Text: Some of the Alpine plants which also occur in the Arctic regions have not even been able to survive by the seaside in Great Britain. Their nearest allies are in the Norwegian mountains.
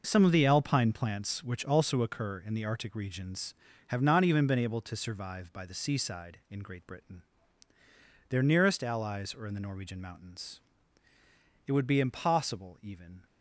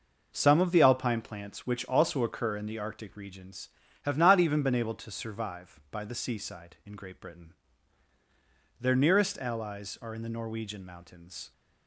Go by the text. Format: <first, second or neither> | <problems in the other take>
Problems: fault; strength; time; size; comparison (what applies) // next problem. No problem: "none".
second | goes on to say "It would be impossible even"; from 11.6 s on; 1.6 s long